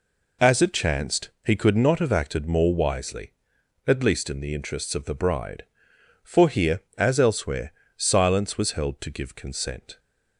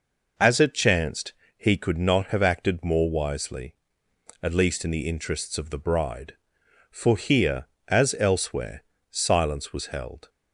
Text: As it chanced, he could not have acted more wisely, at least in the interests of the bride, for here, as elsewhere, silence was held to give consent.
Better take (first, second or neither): first